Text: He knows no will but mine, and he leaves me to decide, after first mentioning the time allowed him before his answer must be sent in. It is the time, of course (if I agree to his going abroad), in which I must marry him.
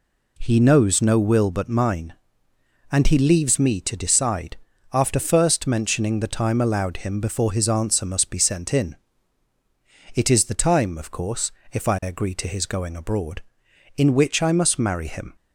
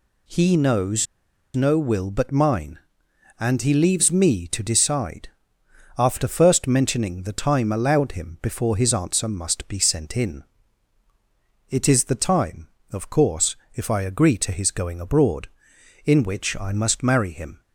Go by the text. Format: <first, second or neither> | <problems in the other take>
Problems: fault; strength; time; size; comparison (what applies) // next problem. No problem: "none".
first | pauses between "knows" and "no"; noticeable; at 1.0 s; 0.49 s long